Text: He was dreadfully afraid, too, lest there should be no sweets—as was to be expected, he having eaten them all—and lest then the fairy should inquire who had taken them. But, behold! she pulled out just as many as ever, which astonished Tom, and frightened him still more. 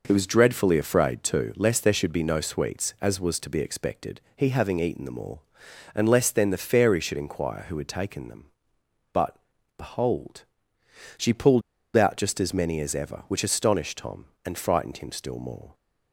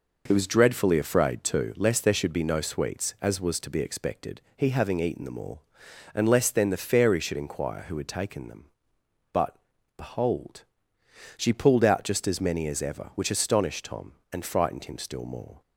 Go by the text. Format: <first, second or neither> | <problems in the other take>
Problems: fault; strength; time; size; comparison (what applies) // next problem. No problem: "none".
second | pauses between "pulled" and "out"; slight; at 11.6 s; 0.32 s long